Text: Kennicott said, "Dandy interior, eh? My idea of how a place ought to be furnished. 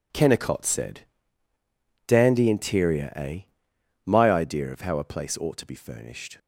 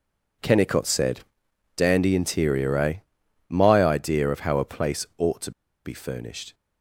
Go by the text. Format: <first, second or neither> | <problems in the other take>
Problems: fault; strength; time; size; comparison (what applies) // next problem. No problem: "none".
first | pauses between "to" and "be"; slight; at 5.5 s; 0.34 s long